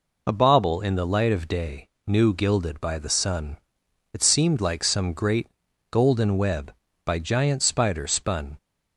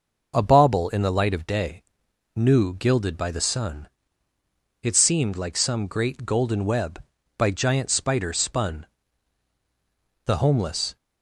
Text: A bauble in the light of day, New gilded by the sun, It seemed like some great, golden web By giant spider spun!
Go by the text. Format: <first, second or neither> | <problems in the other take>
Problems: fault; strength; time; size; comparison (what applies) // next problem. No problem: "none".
first | goes on to say "The homeless"; noticeable; from 10.2 s on; 0.72 s long